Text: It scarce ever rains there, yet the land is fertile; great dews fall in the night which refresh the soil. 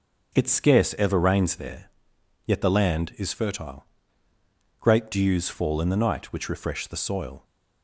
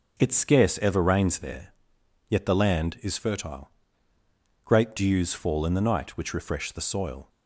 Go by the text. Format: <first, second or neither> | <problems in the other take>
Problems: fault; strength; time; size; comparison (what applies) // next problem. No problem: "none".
neither | starts louder than the rest; the same in both